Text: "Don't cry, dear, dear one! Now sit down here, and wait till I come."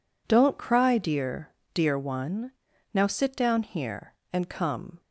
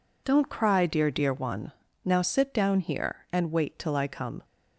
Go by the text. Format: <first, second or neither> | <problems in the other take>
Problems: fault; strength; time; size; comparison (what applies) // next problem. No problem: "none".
second | skips "wait till I"; at 4.4 s